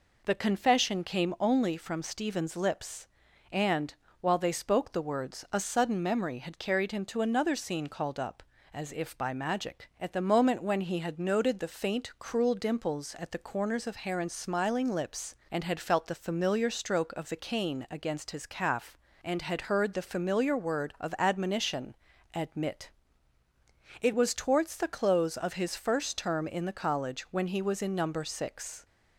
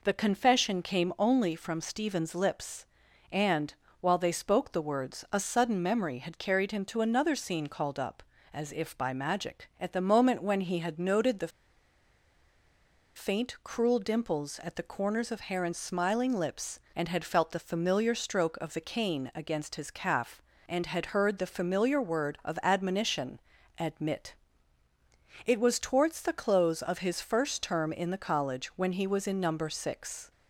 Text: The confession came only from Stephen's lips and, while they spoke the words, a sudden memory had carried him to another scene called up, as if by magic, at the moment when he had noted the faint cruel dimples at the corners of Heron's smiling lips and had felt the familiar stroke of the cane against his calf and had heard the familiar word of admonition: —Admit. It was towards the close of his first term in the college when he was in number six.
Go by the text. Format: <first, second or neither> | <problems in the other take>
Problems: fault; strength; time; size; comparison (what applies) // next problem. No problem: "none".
first | pauses between "the" and "faint"; strong; at 11.5 s; 1.6 s long